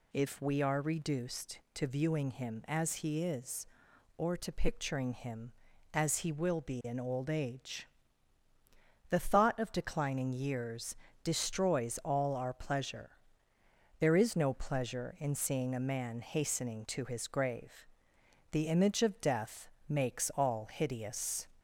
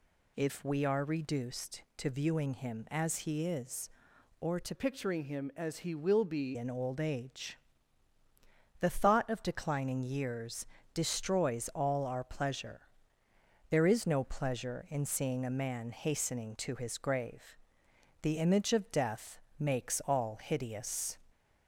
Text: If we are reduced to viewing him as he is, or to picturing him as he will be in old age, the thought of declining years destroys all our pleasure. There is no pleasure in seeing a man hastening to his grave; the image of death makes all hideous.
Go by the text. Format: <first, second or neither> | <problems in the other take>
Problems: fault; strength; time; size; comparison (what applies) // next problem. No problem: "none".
first | changes voice from "picturing" to "be"; from 4.7 to 6.5 s; 1.8 s long // pauses between "years" and "destroys"; slight; at 10.6 s; 0.26 s long; slight in the first // pauses between "death" and "makes"; slight; at 19.4 s; 0.18 s long; slight in the first